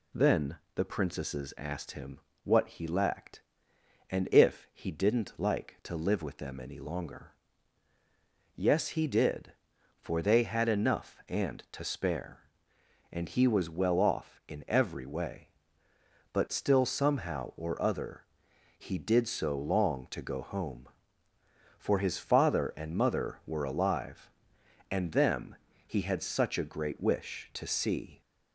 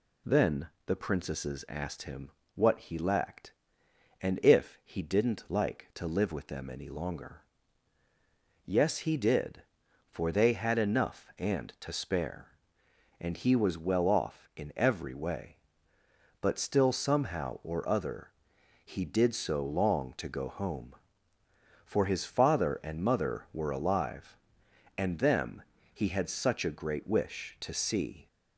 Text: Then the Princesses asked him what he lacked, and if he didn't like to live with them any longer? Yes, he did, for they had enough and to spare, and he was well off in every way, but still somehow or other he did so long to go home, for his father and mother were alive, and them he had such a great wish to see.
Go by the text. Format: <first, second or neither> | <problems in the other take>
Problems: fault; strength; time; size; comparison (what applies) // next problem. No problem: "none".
neither | pauses between "Then" and "the"; slight; the same in both // pauses between "him" and "what"; slight; the same in both // pauses between "other" and "he"; noticeable; the same in both // pauses between "them" and "he"; slight; the same in both